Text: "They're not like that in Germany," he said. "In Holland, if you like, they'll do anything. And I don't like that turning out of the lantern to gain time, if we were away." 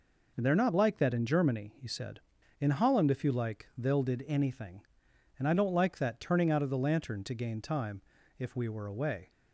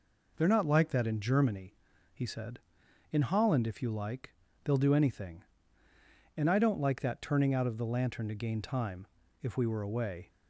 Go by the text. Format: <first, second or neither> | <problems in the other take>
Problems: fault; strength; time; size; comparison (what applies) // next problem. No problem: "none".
second | says "did" for "do"; at 4.0 s